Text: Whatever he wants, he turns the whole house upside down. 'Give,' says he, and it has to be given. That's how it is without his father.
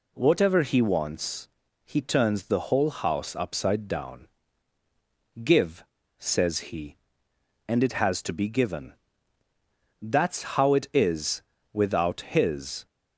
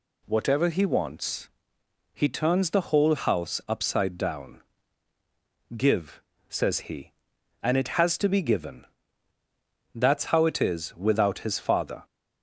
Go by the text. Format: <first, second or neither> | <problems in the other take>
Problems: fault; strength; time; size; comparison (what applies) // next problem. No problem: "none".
second | pauses between "is" and "without"; slight; at 11.4 s; 0.32 s long // stops before "father"; at 12.8 s